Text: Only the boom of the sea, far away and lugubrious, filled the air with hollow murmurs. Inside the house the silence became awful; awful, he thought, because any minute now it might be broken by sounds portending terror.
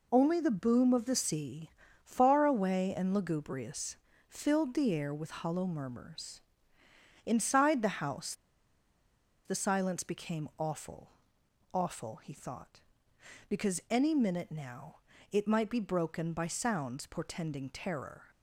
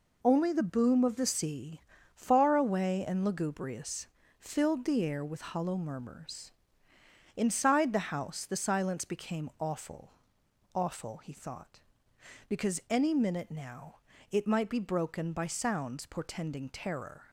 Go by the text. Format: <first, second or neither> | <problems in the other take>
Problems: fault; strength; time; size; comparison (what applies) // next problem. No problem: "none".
second | pauses between "house" and "the"; at 8.3 s; 1.1 s long // pauses between "now" and "it"; slight; at 15.0 s; 0.32 s long; slight in the second